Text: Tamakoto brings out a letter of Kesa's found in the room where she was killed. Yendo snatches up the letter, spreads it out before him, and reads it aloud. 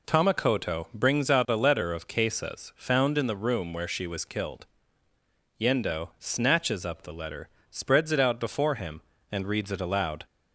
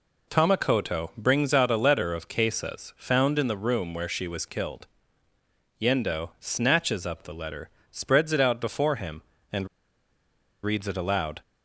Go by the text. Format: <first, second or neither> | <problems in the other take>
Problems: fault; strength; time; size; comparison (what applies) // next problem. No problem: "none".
first | pauses between "and" and "reads"; noticeable; at 9.6 s; 0.97 s long